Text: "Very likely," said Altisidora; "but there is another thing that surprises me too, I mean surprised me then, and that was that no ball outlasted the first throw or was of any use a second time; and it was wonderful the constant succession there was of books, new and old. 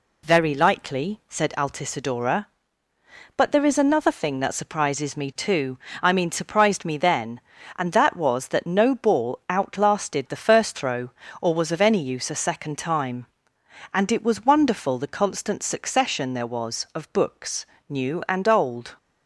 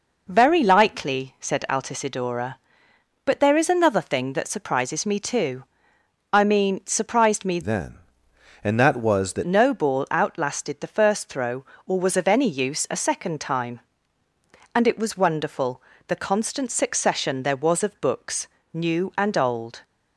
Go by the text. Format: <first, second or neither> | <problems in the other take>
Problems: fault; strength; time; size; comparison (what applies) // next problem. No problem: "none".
first | changes voice from "then" to "that"; from 7.6 to 9.4 s; 1.8 s long // pauses between "wonderful" and "the"; slight; at 15.8 s; 0.26 s long